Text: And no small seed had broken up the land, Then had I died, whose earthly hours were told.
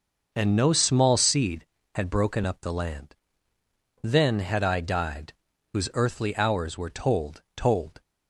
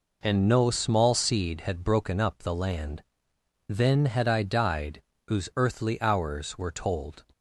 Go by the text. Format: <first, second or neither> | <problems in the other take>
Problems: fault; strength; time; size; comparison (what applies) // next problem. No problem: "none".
second | says "told" twice; at 7.5 s